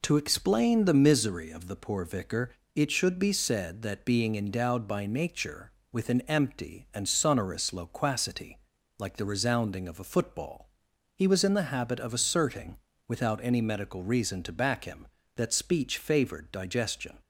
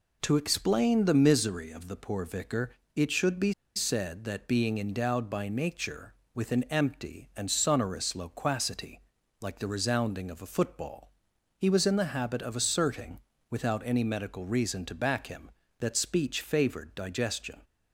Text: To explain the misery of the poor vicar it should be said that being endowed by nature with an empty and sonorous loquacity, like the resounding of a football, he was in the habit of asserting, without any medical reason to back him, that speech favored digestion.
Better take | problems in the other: first | pauses between "vicar" and "it"; slight; at 2.7 s; 0.18 s long; slight in the first // pauses between "be" and "said"; slight; at 3.5 s; 0.22 s long

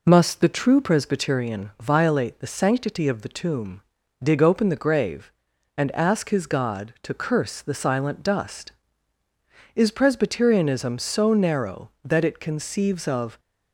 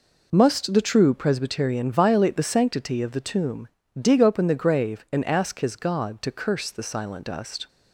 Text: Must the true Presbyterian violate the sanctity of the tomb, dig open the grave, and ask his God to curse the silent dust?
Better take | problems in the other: second | goes on to say "Is Presbyterianism so narrow that it conceives of"; strong; from 9.7 s on; 3.6 s long

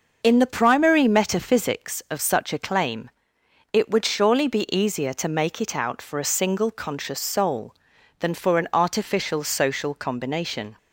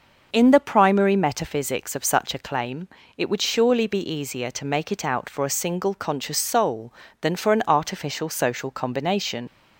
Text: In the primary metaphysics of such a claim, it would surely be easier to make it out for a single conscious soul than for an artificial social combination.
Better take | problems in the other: first | starts louder than the rest; until 1.3 s; 6 dB; noticeable in the first // leaves "combination" unfinished; at 9.4 s; 65 ms

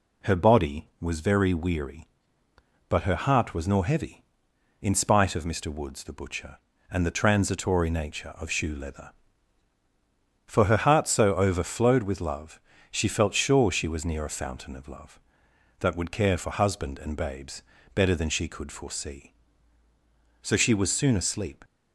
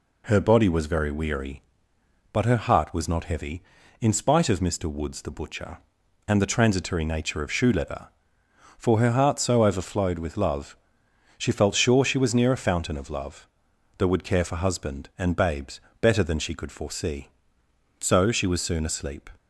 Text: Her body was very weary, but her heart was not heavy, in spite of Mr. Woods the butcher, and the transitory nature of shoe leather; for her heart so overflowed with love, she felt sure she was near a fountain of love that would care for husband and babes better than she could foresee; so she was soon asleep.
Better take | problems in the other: second | says "nor" for "not"; at 3.6 s // pauses between "babes" and "better"; slight; at 17.6 s; 0.32 s long; slight in the second

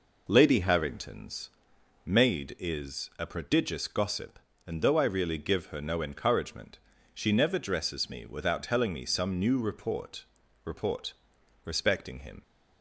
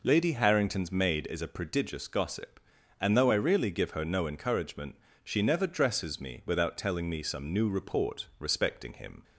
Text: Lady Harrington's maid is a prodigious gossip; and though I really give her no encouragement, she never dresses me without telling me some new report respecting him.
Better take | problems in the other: second | pauses between "Harrington's" and "maid"; noticeable; at 1.5 s; 0.56 s long // says "report" twice; at 10.6 s

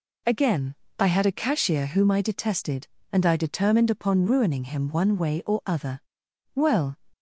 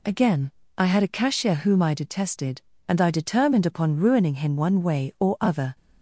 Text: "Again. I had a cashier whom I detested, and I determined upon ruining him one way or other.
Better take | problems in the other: second | goes on to say "Well"; slight; from 6.5 s on; 0.44 s long

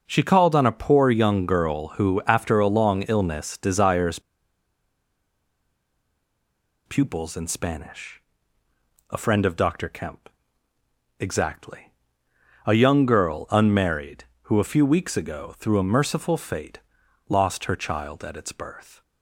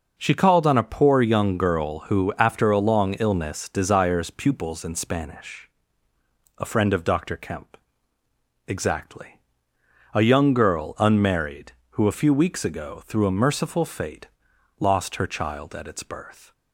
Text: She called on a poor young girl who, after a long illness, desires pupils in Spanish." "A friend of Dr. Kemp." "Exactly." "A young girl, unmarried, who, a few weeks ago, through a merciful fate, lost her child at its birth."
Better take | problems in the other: second | pauses between "desires" and "pupils"; strong; at 4.1 s; 2.6 s long

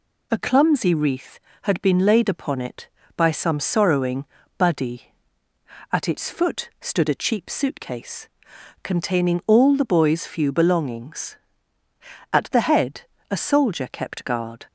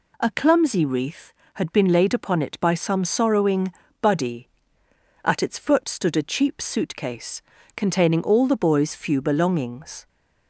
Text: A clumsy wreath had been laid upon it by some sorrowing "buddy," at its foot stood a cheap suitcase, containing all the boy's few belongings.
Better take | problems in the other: second | pauses between "sorrowing" and "buddy"; slight; at 4.2 s; 0.32 s long; slight in the second // goes on to say "At the head a soldier kept guard"; strong; from 12.3 s on; 2.3 s long

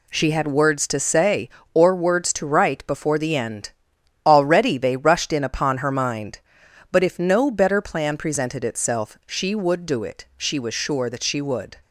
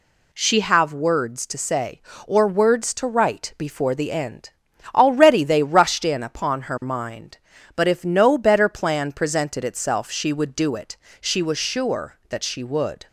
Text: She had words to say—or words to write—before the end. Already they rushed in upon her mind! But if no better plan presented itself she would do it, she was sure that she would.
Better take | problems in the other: first | says "have" for "had"; at 0.6 s

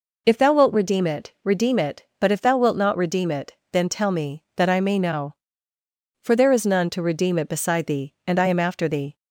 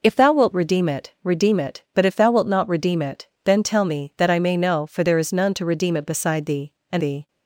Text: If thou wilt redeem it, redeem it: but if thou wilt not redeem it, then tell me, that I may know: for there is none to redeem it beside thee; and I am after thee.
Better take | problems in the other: first | skips "I am after"; at 7.0 s

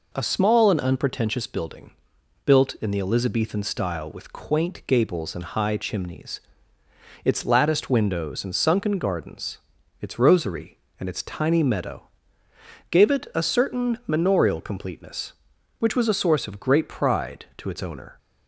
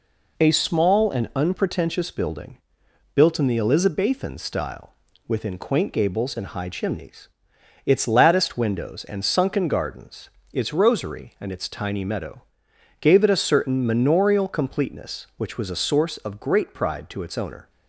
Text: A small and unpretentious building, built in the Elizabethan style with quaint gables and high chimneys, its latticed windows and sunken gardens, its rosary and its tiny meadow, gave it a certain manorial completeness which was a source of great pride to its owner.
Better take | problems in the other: first | says "within" for "with"; at 5.2 s

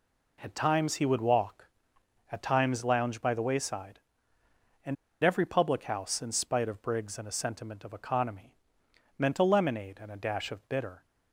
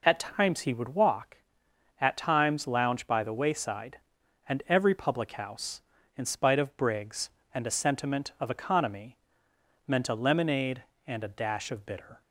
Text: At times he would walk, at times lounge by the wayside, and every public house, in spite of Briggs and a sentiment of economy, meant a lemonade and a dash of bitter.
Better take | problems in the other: second | pauses between "and" and "every"; slight; at 4.9 s; 0.27 s long

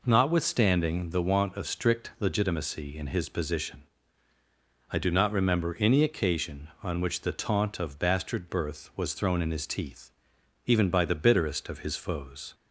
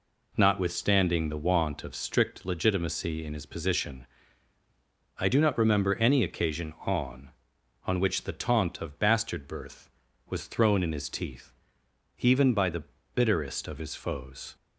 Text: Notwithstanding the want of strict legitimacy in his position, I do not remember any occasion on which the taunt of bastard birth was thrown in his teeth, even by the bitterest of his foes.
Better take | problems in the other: first | says "on" twice; at 7.8 s // pauses between "the" and "bitterest"; slight; at 12.8 s; 0.30 s long

